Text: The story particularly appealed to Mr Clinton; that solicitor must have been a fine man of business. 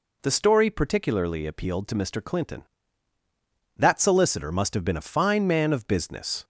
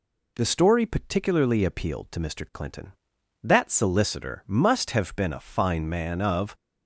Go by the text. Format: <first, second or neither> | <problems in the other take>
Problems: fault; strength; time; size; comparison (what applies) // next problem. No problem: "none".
first | stops before "business"; at 6.5 s